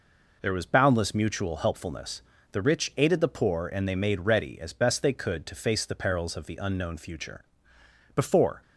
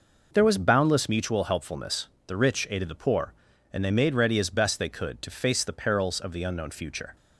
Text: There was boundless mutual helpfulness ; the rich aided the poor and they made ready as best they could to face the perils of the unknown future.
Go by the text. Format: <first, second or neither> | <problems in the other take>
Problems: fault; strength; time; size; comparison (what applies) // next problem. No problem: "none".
second | goes on to say "Before"; slight; from 8.1 s on; 0.46 s long